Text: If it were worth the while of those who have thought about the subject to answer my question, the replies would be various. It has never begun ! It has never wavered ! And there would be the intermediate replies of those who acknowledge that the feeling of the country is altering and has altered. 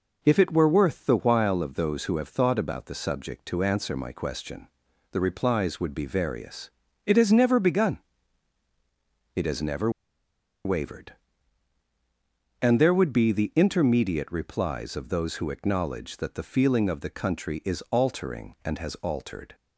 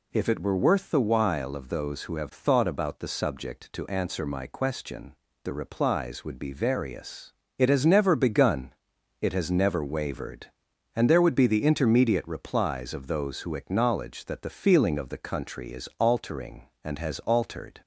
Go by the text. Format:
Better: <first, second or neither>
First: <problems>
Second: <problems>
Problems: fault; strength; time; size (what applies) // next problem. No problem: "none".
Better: second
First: pauses between "never" and "wavered"; noticeable; at 9.8 s; 0.75 s long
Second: none